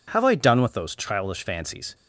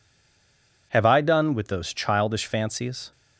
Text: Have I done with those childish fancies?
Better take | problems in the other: first | stays silent before the first word; slight; until 0.9 s; 0.9 s long

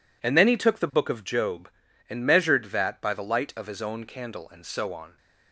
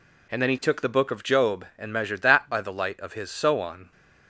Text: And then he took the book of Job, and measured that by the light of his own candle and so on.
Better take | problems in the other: first | skips "own candle and"; at 3.2 s

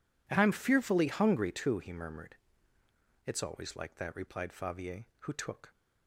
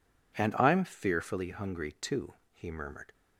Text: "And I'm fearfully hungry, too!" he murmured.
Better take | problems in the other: second | goes on to say "It's always like that replied Favier who took"; strong; from 3.2 s on; 2.4 s long

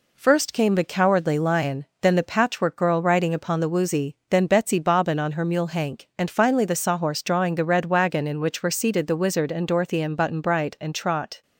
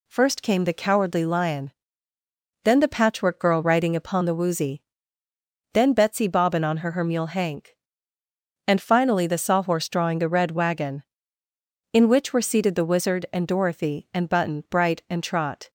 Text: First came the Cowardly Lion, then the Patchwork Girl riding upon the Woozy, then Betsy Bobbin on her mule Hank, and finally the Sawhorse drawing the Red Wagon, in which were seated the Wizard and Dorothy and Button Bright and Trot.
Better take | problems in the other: first | says "her" twice; at 6.9 s

